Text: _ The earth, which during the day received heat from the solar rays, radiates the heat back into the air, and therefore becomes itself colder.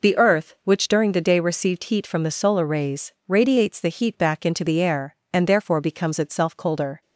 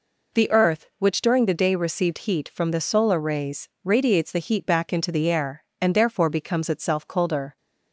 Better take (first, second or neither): neither